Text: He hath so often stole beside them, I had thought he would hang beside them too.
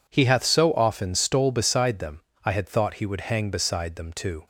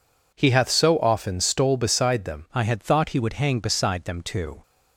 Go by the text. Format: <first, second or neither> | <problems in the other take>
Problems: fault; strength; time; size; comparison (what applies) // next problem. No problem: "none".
first | changes voice at "I"; from 2.5 s on; 2.1 s long